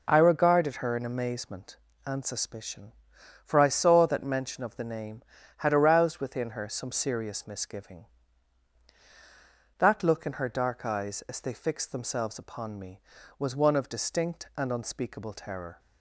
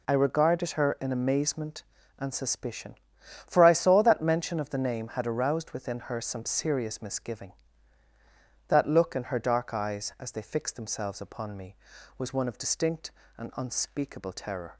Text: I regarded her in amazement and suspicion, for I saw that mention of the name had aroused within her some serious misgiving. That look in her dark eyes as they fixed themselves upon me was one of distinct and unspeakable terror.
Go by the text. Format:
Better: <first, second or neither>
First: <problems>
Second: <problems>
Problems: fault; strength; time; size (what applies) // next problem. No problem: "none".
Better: neither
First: none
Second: none